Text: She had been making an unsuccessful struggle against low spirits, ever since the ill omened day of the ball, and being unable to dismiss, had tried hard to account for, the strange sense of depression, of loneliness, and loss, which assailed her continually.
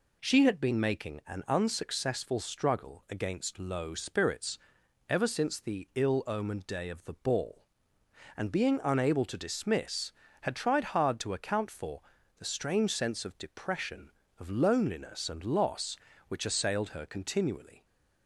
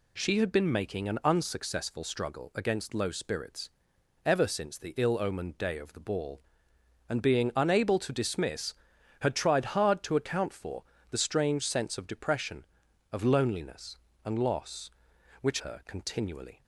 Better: first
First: none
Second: skips "assailed"; at 15.5 s

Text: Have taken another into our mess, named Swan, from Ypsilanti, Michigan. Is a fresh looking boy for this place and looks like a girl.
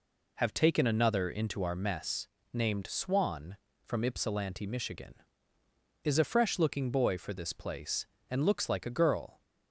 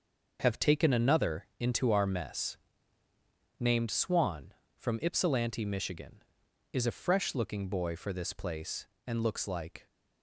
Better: first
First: none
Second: starts louder than the rest; noticeable; until 1.4 s; 6 dB // stops before "a girl"; at 9.8 s

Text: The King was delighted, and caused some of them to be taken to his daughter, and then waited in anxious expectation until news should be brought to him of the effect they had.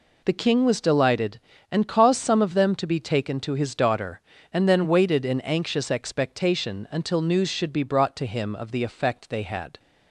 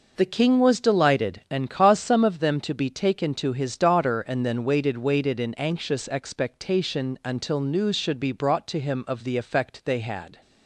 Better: first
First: none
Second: says "waited" twice; at 4.9 s

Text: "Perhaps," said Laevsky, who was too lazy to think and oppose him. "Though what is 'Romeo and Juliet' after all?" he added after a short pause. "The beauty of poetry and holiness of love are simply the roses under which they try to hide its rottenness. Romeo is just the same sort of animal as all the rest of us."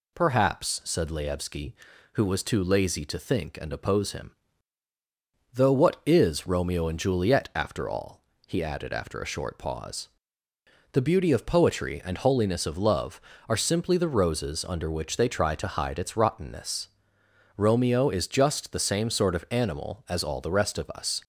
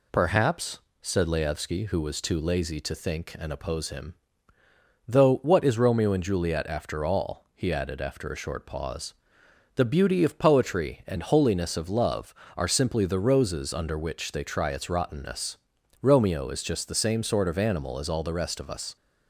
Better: first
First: none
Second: skips "to hide"; at 14.6 s

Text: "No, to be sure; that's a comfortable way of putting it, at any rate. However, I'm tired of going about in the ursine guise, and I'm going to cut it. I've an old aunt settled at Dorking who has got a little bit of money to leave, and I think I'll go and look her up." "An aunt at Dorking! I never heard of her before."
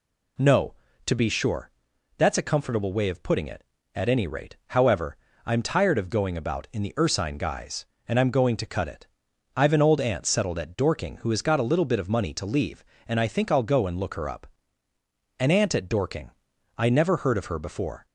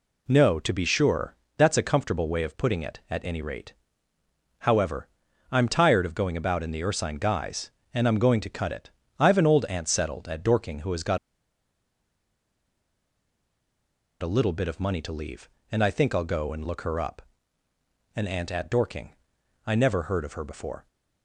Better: first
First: none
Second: pauses between "got" and "a"; strong; at 11.1 s; 3.0 s long

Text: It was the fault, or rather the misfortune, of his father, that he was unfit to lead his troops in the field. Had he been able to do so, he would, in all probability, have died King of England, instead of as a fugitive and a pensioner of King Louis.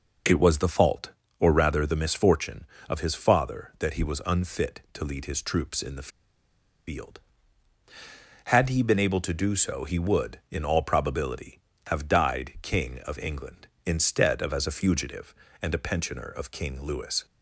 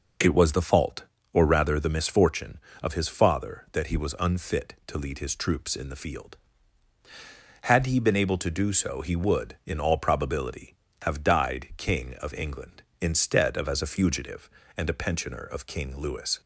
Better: second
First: pauses between "the" and "field"; noticeable; at 6.0 s; 0.78 s long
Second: none

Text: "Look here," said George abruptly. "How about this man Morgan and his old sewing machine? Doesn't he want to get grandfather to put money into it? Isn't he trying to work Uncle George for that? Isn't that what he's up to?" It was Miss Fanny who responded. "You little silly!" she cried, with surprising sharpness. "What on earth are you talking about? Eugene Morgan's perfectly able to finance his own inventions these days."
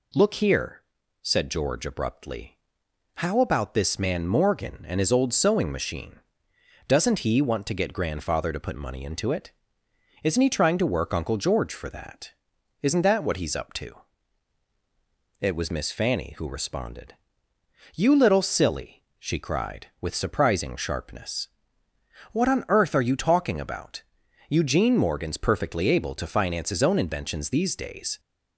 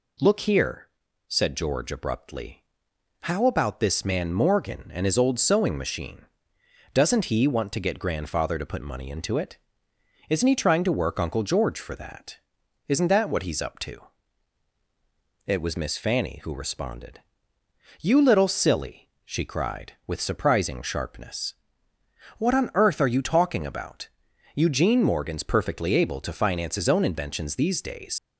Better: first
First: none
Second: leaves "days" unfinished; at 28.1 s; 75 ms

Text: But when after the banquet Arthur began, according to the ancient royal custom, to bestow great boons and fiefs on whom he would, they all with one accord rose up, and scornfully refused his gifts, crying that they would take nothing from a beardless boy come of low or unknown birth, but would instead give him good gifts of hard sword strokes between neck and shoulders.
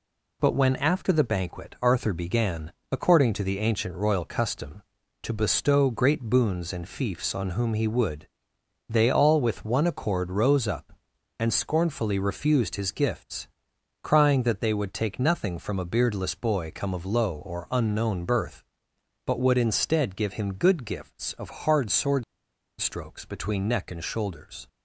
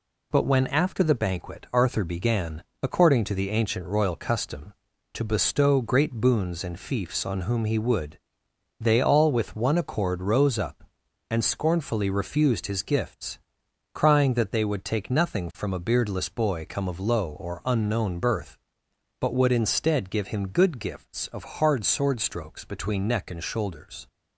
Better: second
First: pauses between "sword" and "strokes"; noticeable; at 22.2 s; 0.55 s long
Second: none

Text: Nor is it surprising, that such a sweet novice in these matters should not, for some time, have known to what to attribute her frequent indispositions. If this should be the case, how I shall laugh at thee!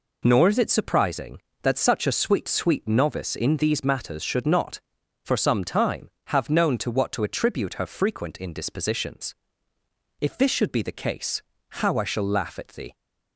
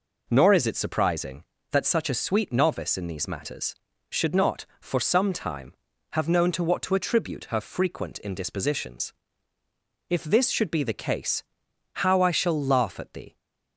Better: second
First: says "sweet" twice; at 2.4 s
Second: none

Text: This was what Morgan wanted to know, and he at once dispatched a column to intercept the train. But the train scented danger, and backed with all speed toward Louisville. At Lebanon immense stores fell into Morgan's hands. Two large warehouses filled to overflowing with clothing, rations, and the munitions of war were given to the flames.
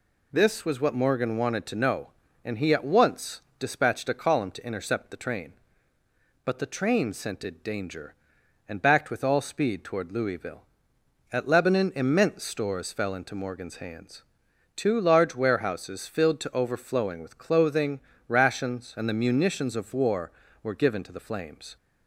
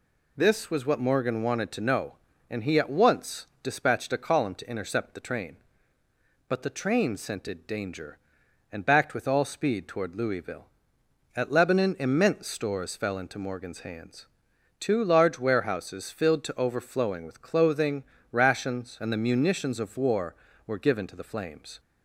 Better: neither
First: pauses between "once" and "dispatched"; slight; at 3.3 s; 0.18 s long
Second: pauses between "once" and "dispatched"; slight; at 3.4 s; 0.16 s long

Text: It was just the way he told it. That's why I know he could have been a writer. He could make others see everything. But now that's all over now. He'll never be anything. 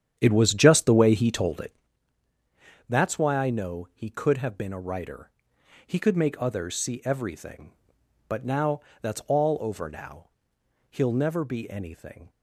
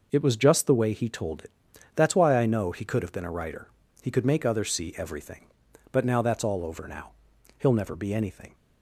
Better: second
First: starts louder than the rest; strong; until 1.9 s; 9 dB // pauses between "now" and "that's"; slight; at 8.7 s; 0.22 s long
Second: none

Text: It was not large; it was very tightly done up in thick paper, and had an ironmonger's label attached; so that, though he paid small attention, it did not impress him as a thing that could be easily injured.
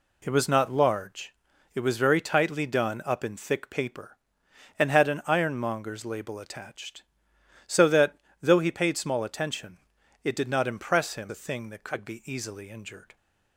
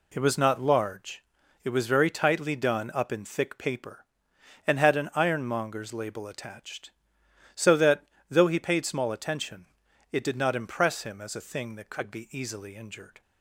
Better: second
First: skips "as"; at 11.2 s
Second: none

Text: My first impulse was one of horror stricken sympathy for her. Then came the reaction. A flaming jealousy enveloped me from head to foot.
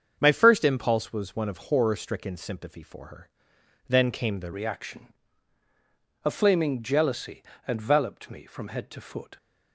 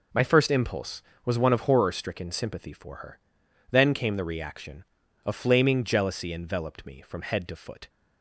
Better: second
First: starts louder than the rest; strong; until 1.2 s; 7 dB // changes voice at "reaction"; from 4.5 s on; 4.8 s long // pauses between "jealousy" and "enveloped"; slight; at 7.4 s; 0.26 s long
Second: none

